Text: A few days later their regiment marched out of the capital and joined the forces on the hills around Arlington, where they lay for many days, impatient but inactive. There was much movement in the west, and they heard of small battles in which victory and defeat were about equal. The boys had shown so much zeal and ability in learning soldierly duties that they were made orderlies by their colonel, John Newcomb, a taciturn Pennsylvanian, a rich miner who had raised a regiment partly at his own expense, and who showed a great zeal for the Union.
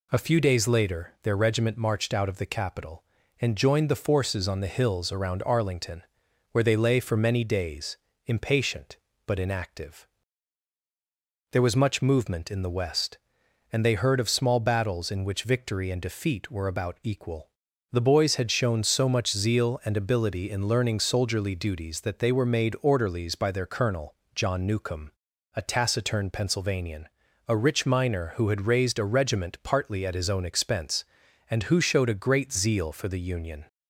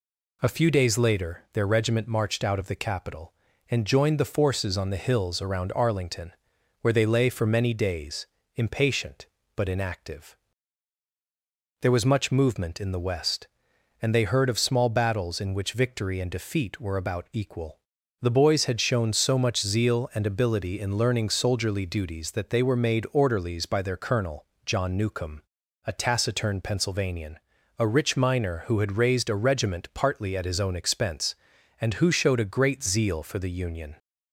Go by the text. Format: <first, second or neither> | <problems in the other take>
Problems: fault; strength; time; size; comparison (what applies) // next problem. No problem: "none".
neither | none